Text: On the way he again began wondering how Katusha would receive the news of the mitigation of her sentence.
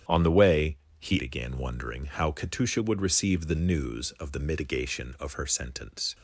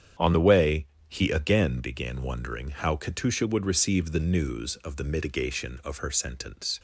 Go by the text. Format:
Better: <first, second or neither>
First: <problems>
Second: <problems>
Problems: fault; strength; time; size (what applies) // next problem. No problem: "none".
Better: second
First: starts louder than the rest; strong; until 1.3 s; 9.5 dB // pauses between "way" and "he"; slight; at 0.7 s; 0.24 s long // skips "again"; at 1.1 s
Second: starts louder than the rest; strong; until 1.4 s; 8.5 dB // pauses between "way" and "he"; slight; at 0.8 s; 0.24 s long